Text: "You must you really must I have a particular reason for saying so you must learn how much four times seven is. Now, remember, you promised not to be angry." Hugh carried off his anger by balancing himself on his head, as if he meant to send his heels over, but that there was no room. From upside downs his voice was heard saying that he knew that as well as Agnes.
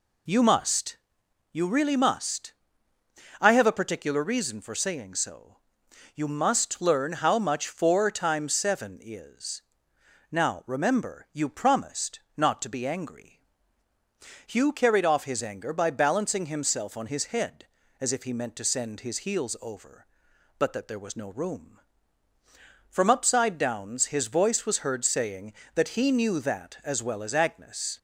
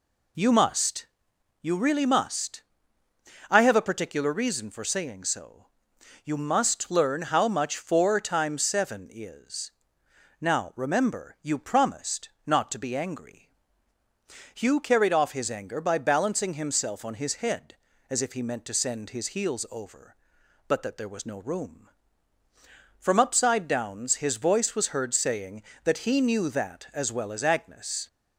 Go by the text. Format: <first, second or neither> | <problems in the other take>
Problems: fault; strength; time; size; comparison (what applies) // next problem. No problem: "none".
neither | pauses between "must" and "you"; noticeable; the same in both // pauses between "must" and "I"; noticeable; the same in both // pauses between "so" and "you"; noticeable; the same in both // pauses between "promised" and "not"; slight; the same in both